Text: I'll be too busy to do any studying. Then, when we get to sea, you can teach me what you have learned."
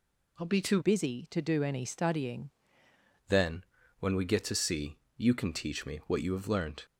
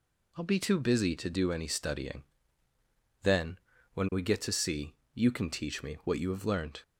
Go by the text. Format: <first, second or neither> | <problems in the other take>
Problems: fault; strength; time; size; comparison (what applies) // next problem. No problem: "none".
second | changes voice from "busy" to "studying"; from 0.8 to 2.4 s; 1.6 s long